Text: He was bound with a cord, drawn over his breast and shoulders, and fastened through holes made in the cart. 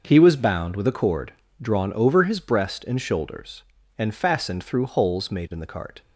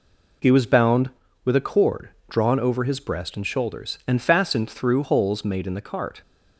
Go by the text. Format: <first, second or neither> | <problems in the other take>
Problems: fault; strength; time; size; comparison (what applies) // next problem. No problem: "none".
neither | none